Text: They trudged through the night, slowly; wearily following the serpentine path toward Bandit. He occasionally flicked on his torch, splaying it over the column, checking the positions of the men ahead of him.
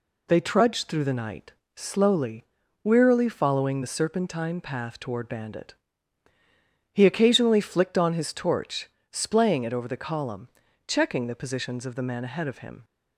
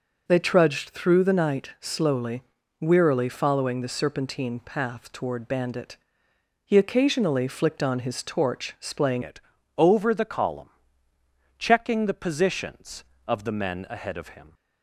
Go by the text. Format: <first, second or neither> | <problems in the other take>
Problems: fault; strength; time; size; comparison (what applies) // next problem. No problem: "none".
first | changes voice at "it"; from 9.2 s on; 5.3 s long // pauses between "it" and "over"; slight; at 9.4 s; 0.36 s long